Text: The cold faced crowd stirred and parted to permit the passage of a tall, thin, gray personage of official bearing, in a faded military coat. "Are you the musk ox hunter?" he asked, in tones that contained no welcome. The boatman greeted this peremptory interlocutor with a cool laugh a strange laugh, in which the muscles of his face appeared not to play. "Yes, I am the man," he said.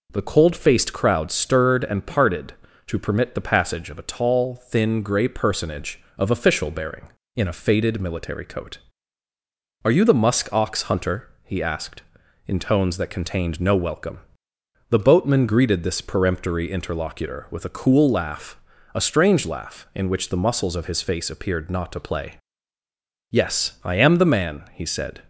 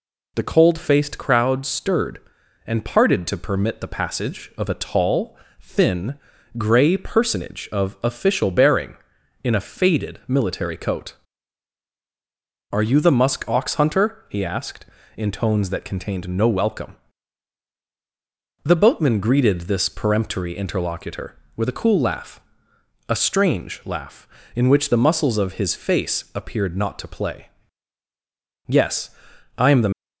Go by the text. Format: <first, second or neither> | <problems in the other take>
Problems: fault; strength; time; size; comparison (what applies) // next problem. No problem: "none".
first | pauses between "laugh" and "a"; noticeable; at 22.3 s; 0.70 s long; also in the first // stops before "man he said"; at 29.9 s